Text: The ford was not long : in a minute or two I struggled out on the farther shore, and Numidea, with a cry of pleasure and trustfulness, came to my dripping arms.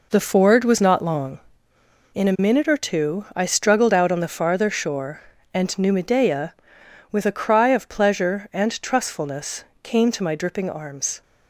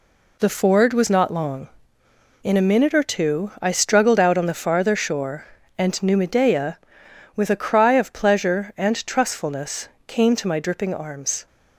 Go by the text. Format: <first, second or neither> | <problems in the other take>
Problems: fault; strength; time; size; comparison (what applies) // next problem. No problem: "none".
second | starts louder than the rest; noticeable; until 1.4 s; 4.5 dB